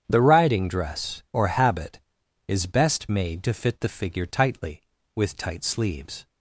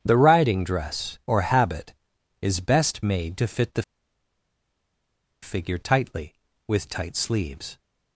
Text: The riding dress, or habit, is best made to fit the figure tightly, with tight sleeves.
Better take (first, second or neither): first